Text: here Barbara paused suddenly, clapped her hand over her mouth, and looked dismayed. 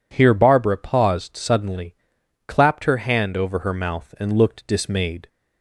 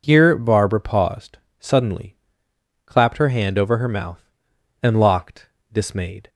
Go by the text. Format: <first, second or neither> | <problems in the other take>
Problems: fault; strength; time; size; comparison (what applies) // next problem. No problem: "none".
first | pauses between "paused" and "suddenly"; slight; at 1.3 s; 0.20 s long // says "locked" for "looked"; at 5.0 s